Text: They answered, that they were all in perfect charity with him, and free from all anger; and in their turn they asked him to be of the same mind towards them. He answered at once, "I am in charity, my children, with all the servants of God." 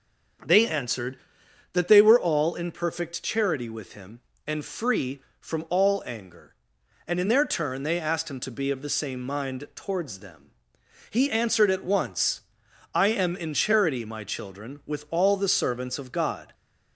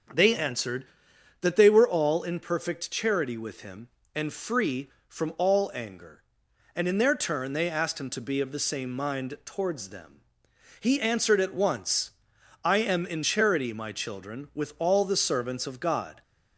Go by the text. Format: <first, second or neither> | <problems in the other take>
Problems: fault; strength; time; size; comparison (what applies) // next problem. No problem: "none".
neither | starts louder than the rest; the same in both